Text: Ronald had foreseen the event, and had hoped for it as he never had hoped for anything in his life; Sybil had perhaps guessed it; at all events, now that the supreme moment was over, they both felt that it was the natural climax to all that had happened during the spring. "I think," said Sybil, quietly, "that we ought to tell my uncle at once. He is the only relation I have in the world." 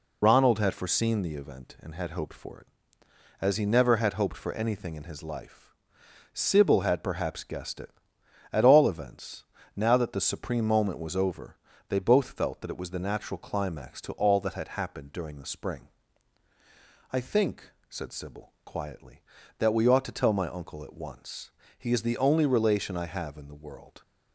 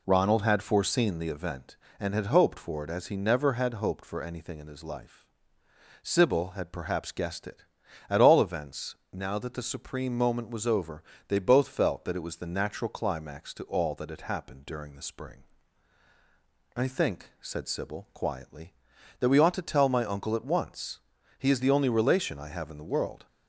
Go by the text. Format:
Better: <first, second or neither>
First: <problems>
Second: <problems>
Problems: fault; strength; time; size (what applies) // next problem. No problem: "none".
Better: second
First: loses the start of "Ronald"; at 0.2 s; 50 ms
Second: none